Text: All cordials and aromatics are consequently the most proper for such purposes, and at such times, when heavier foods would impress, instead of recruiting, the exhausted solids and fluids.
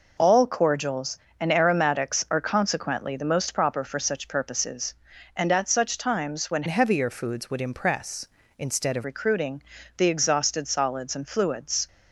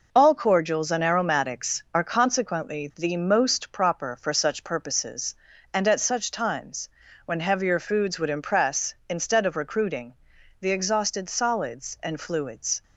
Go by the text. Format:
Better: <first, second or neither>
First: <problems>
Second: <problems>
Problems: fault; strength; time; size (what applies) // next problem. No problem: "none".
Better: second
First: changes voice from "heavier" to "of"; from 6.6 to 9.0 s; 2.4 s long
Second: none